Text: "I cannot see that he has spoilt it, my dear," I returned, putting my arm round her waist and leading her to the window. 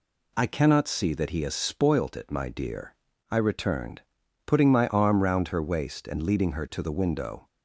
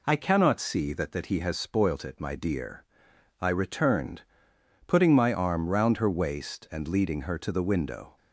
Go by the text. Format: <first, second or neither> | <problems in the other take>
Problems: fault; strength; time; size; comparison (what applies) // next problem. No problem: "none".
first | says "that" twice; at 1.1 s